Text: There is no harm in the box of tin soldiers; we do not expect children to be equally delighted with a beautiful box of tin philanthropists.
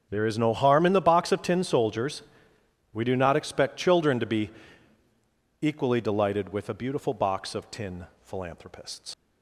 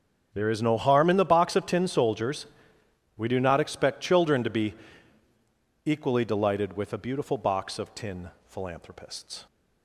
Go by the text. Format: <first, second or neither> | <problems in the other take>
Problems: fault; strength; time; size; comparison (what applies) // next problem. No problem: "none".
second | starts louder than the rest; strong; until 1.1 s; 7 dB; strong in the second // pauses between "be" and "equally"; at 4.5 s; 1.1 s long; also in the second // pauses between "tin" and "philanthropists"; slight; at 8.0 s; 0.16 s long; slight in the second // leaves "philanthropists" unfinished; at 9.1 s; 85 ms